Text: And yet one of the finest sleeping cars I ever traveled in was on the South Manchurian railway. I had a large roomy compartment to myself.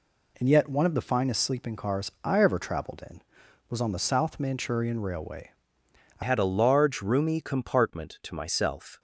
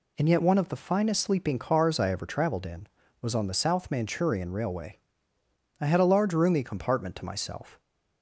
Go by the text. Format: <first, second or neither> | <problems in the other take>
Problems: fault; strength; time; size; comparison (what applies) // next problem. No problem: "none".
second | changes voice at "had"; from 6.2 s on; 2.7 s long